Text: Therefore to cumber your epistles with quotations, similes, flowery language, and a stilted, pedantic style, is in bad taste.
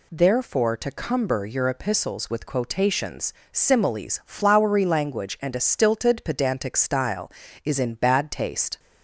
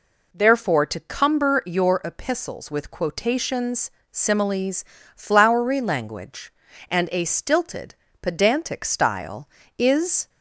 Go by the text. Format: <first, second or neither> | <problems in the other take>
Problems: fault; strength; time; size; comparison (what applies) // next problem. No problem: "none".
first | stops before "in bad taste"; at 10.2 s